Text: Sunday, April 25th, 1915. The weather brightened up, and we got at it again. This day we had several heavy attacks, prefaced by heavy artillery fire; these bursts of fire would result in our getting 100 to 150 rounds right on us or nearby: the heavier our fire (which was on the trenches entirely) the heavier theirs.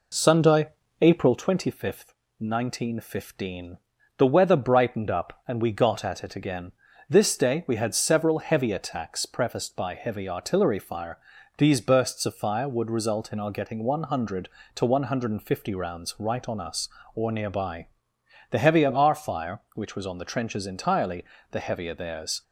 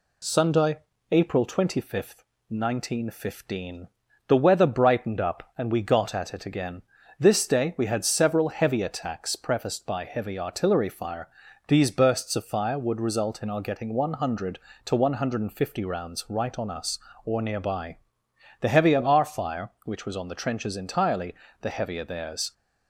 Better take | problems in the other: second | starts louder than the rest; until 1.4 s; 3.5 dB

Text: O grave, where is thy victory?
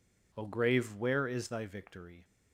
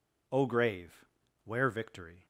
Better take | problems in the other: first | skips "is thy"; at 1.6 s

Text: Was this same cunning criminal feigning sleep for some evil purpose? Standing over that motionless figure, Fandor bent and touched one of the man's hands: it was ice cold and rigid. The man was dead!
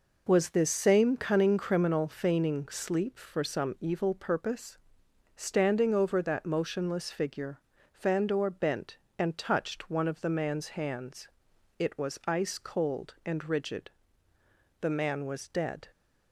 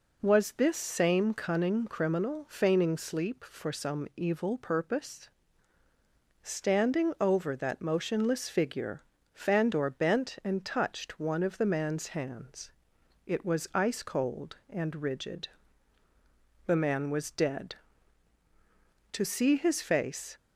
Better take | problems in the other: first | goes on to say "To see his face"; noticeable; from 19.1 s on; 1.2 s long

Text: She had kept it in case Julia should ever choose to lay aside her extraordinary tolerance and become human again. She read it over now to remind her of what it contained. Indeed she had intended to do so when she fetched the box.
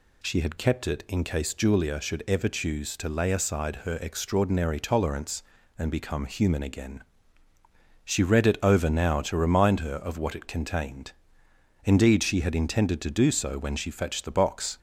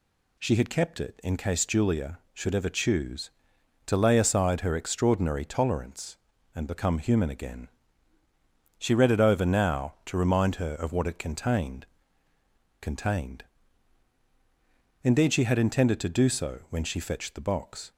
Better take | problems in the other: first | says "contained" twice; at 12.8 s

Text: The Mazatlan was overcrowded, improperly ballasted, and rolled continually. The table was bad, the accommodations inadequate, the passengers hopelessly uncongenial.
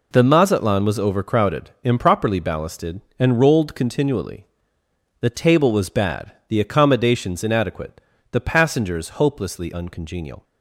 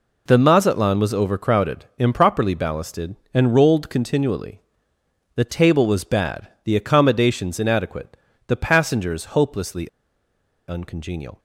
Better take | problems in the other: first | pauses between "hopelessly" and "uncongenial"; noticeable; at 9.8 s; 0.79 s long

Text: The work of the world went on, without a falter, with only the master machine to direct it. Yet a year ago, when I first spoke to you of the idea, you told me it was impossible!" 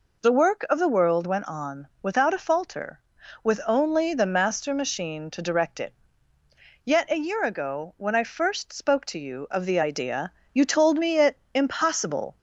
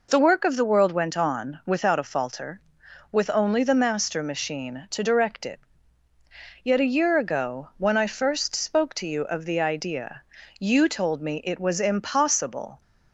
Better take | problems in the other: second | skips "was"; at 11.4 s

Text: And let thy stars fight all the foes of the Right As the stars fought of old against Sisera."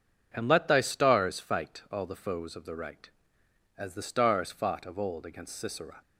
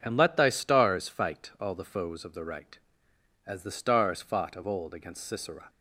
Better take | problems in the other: neither | none

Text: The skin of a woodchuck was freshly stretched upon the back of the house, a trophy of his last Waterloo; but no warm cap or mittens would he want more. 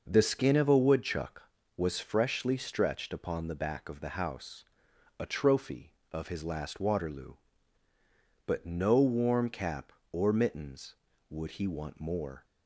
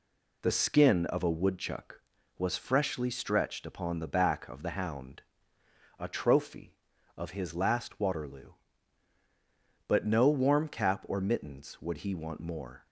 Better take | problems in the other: first | says "hound" for "house"; at 4.7 s

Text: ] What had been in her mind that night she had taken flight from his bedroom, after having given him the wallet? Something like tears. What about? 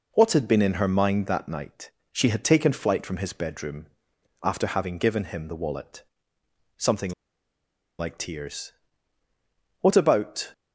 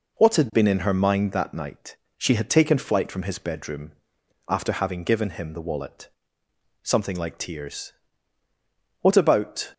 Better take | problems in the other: second | pauses between "night" and "she"; slight; at 1.9 s; 0.20 s long; slight in the second // pauses between "Something" and "like"; noticeable; at 7.1 s; 0.87 s long

